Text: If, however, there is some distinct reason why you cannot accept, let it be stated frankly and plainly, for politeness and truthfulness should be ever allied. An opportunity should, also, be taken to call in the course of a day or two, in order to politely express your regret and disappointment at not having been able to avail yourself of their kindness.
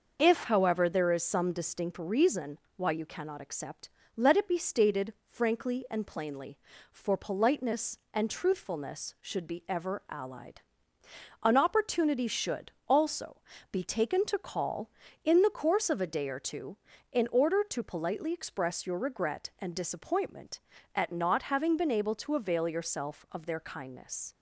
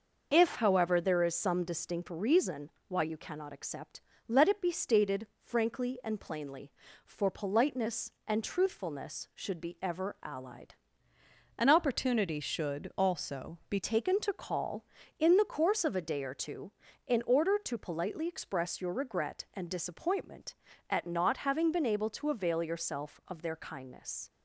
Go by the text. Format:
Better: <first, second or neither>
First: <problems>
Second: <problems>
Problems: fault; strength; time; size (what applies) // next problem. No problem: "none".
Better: first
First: pauses between "reason" and "why"; slight; at 2.5 s; 0.18 s long // pauses between "stated" and "frankly"; slight; at 5.1 s; 0.16 s long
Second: pauses between "reason" and "why"; slight; at 2.7 s; 0.18 s long // pauses between "stated" and "frankly"; slight; at 5.2 s; 0.16 s long // changes voice from "An" to "be"; from 11.5 to 13.7 s; 2.2 s long